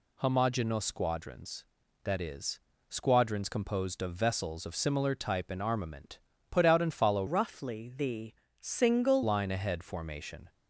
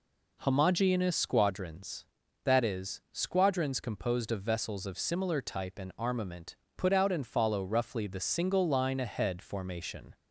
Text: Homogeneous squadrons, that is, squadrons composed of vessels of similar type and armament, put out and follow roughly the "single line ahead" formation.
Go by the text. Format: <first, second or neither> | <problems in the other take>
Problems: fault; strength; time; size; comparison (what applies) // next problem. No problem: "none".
second | changes voice from "roughly" to "single"; from 7.2 to 9.2 s; 2.0 s long // pauses between "the" and "single"; slight; at 8.3 s; 0.28 s long